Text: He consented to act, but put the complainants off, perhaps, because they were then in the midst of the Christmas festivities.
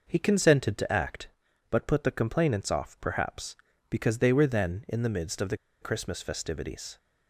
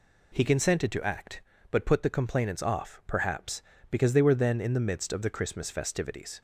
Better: second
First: pauses between "the" and "Christmas"; slight; at 5.5 s; 0.23 s long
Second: none

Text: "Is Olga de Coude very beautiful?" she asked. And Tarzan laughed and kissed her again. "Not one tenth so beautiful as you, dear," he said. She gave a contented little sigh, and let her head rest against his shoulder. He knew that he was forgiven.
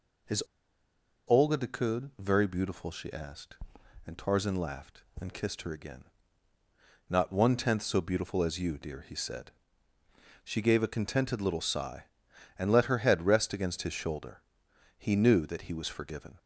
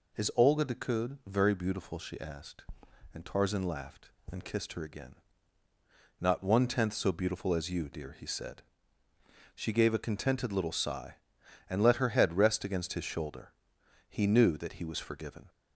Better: second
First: pauses between "Is" and "Olga"; noticeable; at 0.4 s; 0.86 s long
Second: none

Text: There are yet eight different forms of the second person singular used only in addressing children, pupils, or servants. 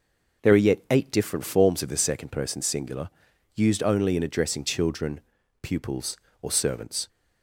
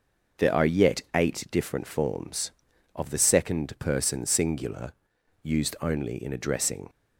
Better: first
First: pauses between "singular" and "used"; at 3.0 s; 0.44 s long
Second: pauses between "singular" and "used"; noticeable; at 4.9 s; 0.50 s long // stops before "children pupils or servants"; at 6.8 s

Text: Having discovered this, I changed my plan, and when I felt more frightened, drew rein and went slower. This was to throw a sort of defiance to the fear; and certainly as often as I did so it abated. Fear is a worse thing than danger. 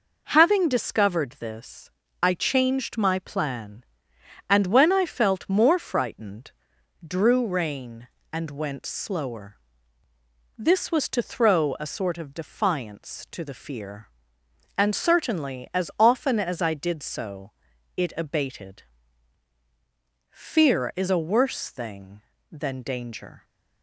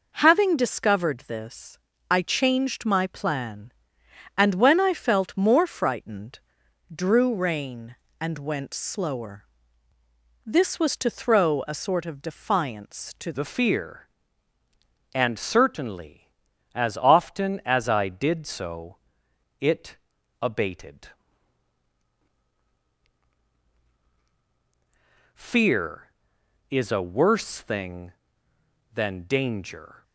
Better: first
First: pauses between "so" and "it"; at 17.5 s; 0.44 s long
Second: changes voice at "the"; from 13.3 s on; 16.7 s long // pauses between "so" and "it"; noticeable; at 18.9 s; 0.64 s long // pauses between "it" and "abated"; noticeable; at 19.9 s; 0.46 s long

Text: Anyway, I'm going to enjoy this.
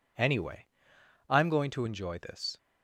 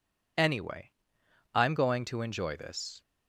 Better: neither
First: none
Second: none

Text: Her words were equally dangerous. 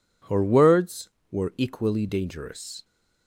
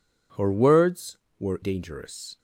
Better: first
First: none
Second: skips "equally"; at 1.6 s

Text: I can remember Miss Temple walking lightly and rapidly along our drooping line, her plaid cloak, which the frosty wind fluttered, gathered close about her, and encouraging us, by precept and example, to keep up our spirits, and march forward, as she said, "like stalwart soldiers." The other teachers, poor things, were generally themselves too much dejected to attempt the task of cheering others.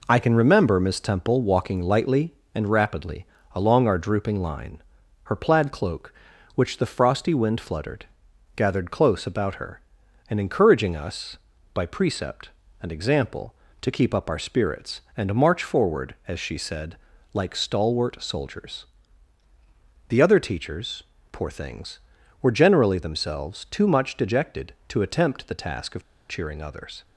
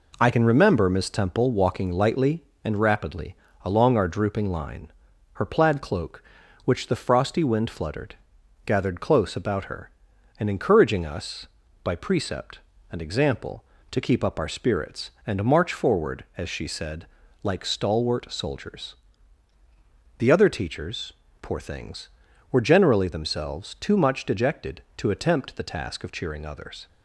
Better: second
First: pauses between "rapidly" and "along"; slight; at 3.2 s; 0.30 s long // pauses between "of" and "cheering"; slight; at 26.0 s; 0.25 s long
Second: pauses between "rapidly" and "along"; slight; at 3.3 s; 0.30 s long

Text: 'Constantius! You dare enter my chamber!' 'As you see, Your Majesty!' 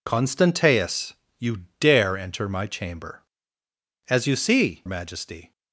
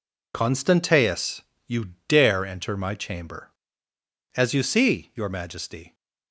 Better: second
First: pauses between "You" and "dare"; slight; at 1.6 s; 0.16 s long // skips "Your"; at 4.8 s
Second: pauses between "You" and "dare"; slight; at 1.9 s; 0.16 s long

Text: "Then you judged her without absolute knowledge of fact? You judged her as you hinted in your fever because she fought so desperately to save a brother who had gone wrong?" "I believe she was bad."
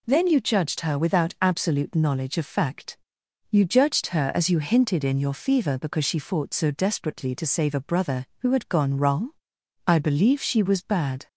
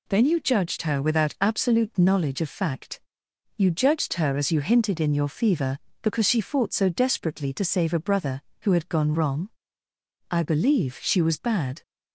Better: neither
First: none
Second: none

